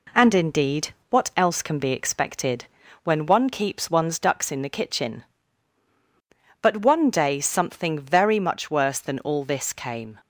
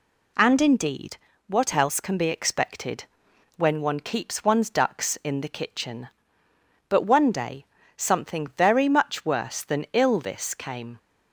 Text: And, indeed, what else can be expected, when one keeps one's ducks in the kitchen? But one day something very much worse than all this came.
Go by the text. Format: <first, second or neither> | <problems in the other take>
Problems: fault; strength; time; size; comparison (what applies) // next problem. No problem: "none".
first | pauses between "day" and "something"; slight; at 7.6 s; 0.30 s long // says "ill" for "all"; at 9.9 s